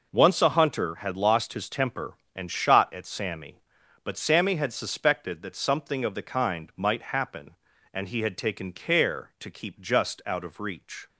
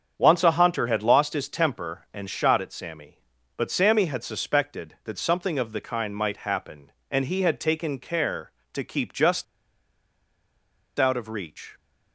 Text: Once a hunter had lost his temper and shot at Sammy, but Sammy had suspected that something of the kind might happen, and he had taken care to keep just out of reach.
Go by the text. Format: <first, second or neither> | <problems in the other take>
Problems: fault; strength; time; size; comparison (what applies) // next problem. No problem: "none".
first | starts louder than the rest; strong; until 1.1 s; 7.5 dB // pauses between "just" and "out"; strong; at 9.4 s; 1.5 s long